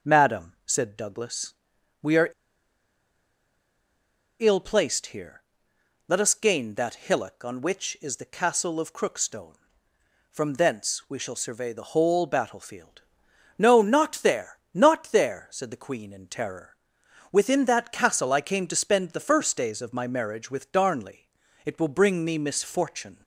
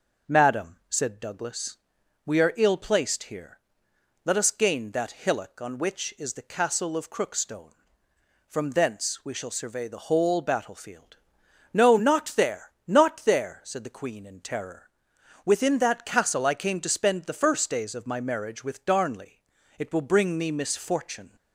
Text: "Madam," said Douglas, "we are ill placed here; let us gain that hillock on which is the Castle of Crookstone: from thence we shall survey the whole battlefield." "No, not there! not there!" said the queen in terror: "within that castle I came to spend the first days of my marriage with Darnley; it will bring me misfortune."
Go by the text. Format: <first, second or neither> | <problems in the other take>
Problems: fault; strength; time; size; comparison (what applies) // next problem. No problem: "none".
second | pauses between "are" and "ill"; strong; at 2.2 s; 2.1 s long